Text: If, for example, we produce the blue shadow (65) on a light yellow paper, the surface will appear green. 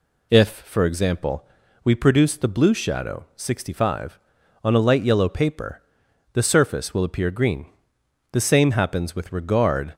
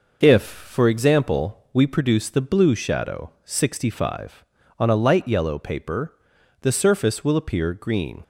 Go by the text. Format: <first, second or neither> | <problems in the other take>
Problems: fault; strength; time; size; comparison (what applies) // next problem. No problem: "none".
second | goes on to say "The same happens with regard"; from 8.3 s on; 1.6 s long